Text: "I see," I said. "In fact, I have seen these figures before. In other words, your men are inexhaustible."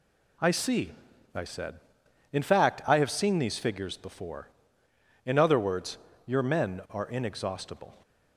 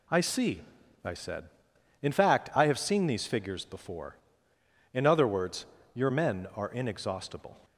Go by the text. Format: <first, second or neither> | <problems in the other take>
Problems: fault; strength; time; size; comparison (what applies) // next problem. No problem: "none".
neither | none